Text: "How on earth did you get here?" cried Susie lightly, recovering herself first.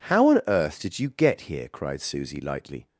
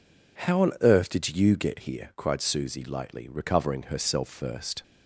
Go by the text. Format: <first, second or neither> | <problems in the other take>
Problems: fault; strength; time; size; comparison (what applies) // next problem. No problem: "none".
second | stops before "recovering herself first"; at 2.8 s